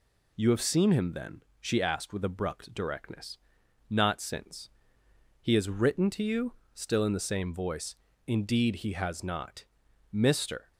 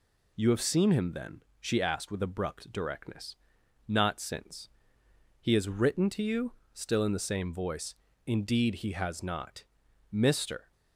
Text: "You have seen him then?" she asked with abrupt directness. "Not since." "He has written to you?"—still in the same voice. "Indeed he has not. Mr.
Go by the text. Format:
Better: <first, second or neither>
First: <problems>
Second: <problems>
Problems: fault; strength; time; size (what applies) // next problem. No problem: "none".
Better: neither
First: none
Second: none